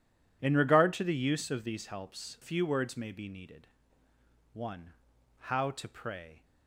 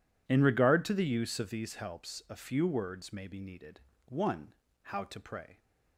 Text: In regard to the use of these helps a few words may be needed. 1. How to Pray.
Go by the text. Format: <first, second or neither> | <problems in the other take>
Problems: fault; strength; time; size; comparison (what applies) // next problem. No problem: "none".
second | skips "a"; at 2.3 s